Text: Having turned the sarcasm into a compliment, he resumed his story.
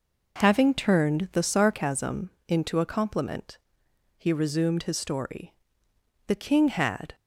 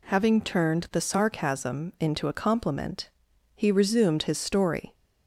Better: second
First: pauses between "sarcasm" and "into"; slight; at 2.2 s; 0.18 s long // goes on to say "The king had"; noticeable; from 6.2 s on; 0.88 s long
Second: none

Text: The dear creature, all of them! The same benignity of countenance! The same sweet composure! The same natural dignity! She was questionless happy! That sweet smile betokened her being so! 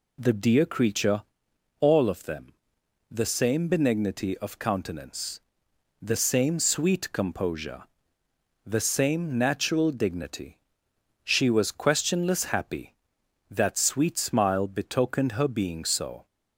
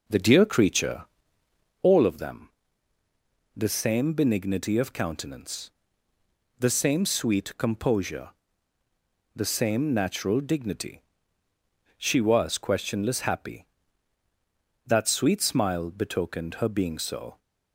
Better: first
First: none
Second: starts louder than the rest; noticeable; until 2.0 s; 5.5 dB

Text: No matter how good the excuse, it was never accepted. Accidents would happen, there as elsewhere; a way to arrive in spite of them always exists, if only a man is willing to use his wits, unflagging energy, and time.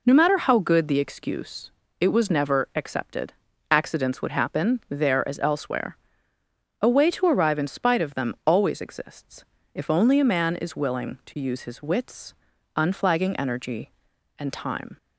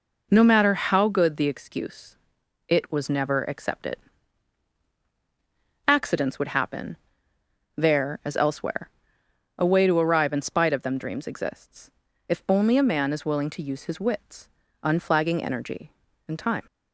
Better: first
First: none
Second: says "dreams" for "always"; at 10.9 s

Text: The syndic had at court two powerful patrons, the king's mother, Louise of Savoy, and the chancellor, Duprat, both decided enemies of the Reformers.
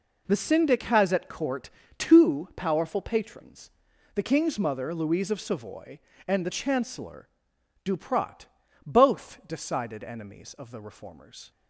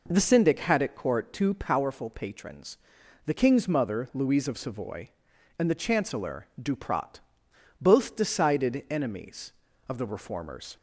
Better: second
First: says "has" for "had"; at 0.8 s // pauses between "court" and "two"; slight; at 1.7 s; 0.28 s long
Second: none

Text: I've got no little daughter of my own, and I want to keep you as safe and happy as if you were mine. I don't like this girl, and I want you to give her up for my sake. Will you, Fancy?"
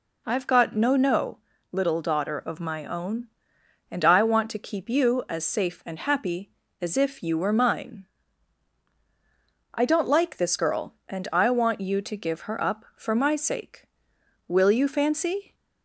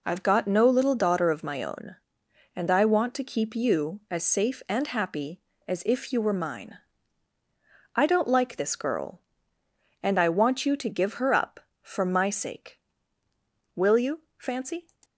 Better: second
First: says "no" twice; at 0.9 s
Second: none

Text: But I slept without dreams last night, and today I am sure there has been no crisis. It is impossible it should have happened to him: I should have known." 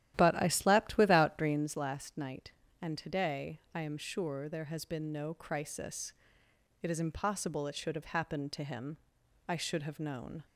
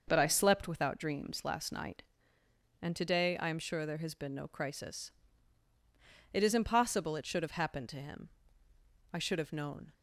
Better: second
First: starts louder than the rest; strong; until 1.8 s; 12.5 dB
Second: none

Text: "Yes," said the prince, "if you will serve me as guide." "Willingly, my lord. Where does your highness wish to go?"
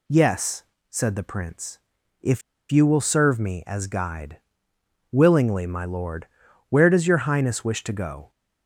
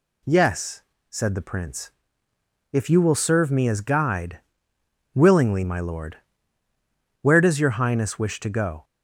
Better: second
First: pauses between "if" and "you"; slight; at 2.4 s; 0.30 s long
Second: none

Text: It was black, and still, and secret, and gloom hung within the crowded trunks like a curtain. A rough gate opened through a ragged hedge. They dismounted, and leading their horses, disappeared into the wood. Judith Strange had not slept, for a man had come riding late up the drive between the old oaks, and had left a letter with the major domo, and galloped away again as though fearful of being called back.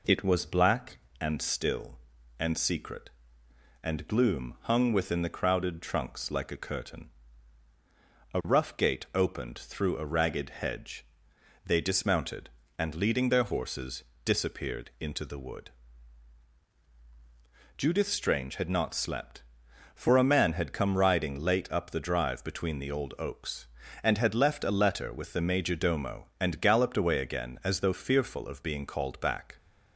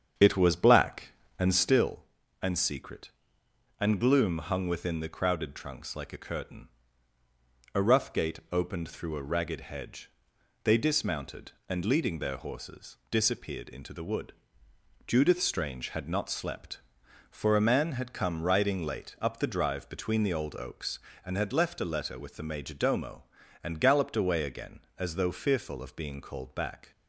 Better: first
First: none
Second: starts louder than the rest; strong; until 1.9 s; 7.5 dB

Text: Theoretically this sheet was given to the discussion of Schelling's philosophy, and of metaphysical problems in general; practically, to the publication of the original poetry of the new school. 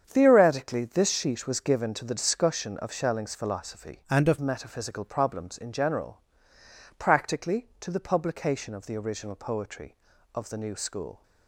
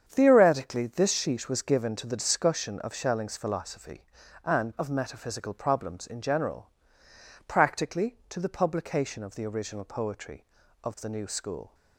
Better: second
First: starts louder than the rest; strong; until 1.0 s; 7.5 dB // changes voice from "and" to "of"; from 4.0 to 4.3 s; 0.3 s long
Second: starts louder than the rest; strong; until 1.0 s; 8 dB

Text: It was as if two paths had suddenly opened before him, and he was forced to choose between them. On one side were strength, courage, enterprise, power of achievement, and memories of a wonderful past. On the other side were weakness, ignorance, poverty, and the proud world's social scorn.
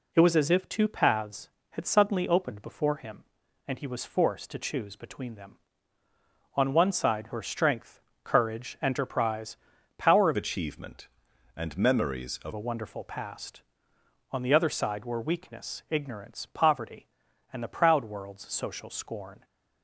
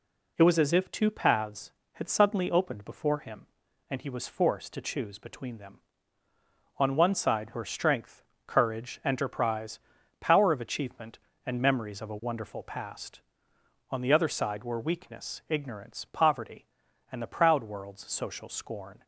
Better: second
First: changes voice from "achievement" to "of"; from 10.3 to 12.5 s; 2.2 s long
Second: none

